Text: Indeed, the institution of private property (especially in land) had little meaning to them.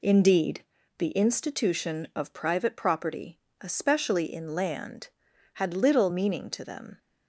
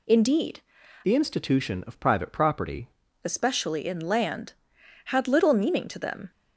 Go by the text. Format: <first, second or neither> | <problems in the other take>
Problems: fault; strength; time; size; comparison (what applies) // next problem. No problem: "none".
first | changes voice from "the" to "property"; from 1.0 to 2.8 s; 1.8 s long